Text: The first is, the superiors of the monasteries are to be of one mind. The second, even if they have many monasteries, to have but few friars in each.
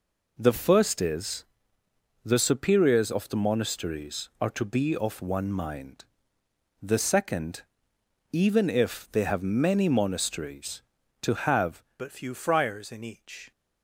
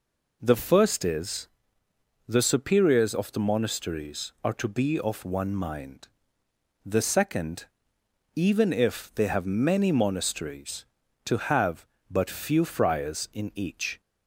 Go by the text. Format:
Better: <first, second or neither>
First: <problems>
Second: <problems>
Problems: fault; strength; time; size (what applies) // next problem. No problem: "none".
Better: second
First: changes voice at "but"; from 11.9 s on; 1.6 s long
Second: none